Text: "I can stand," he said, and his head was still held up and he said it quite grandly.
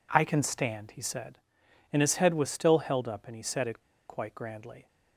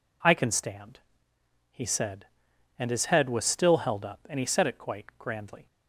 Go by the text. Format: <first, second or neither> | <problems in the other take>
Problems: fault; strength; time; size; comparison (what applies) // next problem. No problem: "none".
second | pauses between "it" and "quite"; slight; at 3.7 s; 0.29 s long